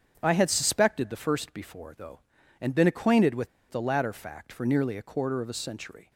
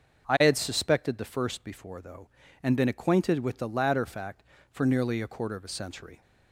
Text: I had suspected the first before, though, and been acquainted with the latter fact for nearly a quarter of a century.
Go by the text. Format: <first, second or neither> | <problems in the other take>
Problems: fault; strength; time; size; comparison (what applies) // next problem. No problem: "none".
second | starts louder than the rest; strong; until 1.2 s; 7.5 dB; noticeable in the second // pauses between "with" and "the"; slight; at 3.4 s; 0.21 s long